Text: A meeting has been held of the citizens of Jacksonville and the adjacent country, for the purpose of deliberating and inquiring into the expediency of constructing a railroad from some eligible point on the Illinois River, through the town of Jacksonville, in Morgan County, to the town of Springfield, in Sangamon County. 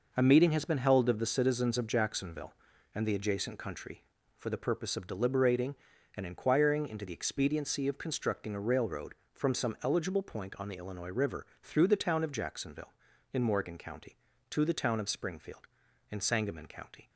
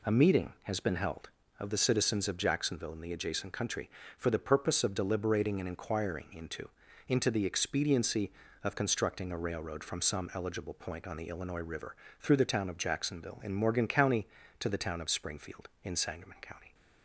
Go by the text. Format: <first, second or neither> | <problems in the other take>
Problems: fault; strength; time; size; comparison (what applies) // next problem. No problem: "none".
first | says "into" twice; at 7.0 s